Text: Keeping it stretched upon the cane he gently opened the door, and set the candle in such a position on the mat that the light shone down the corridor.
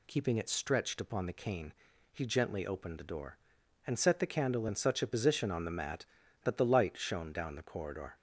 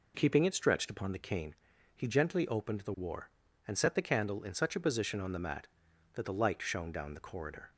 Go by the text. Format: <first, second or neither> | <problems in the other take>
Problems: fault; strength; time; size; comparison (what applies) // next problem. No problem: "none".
first | pauses between "cane" and "he"; at 1.5 s; 0.40 s long; also in the first // says "war" for "door"; at 2.9 s